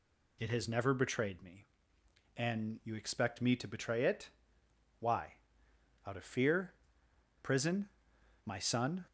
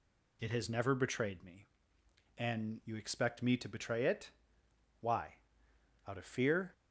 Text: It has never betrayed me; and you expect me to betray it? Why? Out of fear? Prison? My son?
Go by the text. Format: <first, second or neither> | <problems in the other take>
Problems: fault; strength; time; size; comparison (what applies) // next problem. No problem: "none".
first | stops before "Prison My son"; at 6.7 s